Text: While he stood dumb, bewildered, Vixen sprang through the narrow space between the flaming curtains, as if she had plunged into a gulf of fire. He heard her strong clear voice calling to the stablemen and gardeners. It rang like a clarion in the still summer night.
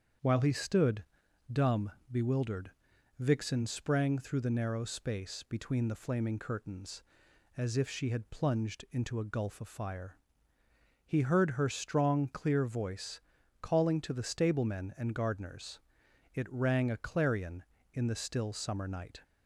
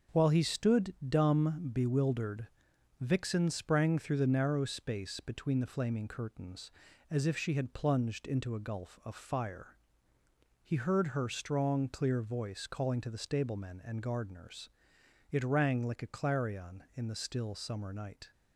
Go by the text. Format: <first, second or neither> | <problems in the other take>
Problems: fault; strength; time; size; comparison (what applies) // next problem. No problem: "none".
second | starts louder than the rest; strong; until 1.6 s; 7.5 dB; strong in the second // pauses between "stood" and "dumb"; noticeable; at 1.0 s; 0.48 s long // pauses between "voice" and "calling"; at 13.2 s; 0.40 s long // skips "like"; at 16.9 s